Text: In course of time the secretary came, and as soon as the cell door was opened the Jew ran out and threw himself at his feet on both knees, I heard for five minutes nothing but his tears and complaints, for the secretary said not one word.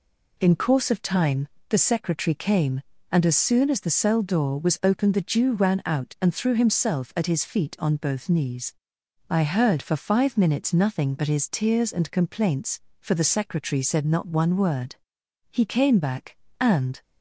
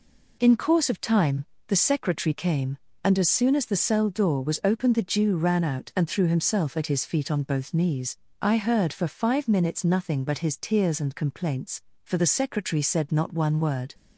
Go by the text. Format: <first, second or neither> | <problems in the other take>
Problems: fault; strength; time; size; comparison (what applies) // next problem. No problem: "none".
second | pauses between "time" and "the"; slight; at 1.4 s; 0.22 s long; slight in the second // goes on to say "He came back and"; from 15.4 s on; 1.5 s long